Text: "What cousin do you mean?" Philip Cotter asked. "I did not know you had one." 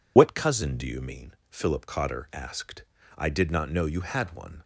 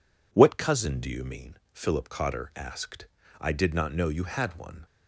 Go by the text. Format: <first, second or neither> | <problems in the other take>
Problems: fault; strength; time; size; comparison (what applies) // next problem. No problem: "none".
second | loses the start of "What"; at 0.1 s; 55 ms